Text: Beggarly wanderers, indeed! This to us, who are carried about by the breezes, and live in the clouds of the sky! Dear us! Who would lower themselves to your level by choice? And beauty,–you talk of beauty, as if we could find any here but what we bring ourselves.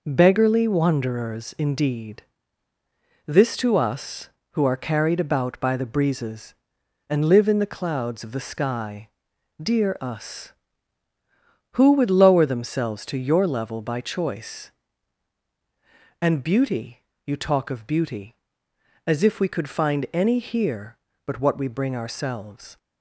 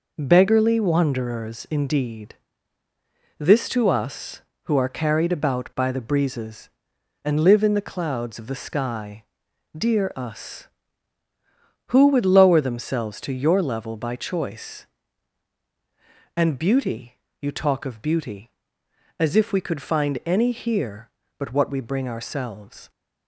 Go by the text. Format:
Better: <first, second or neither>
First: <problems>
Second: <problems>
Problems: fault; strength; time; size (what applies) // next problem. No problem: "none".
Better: neither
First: none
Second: none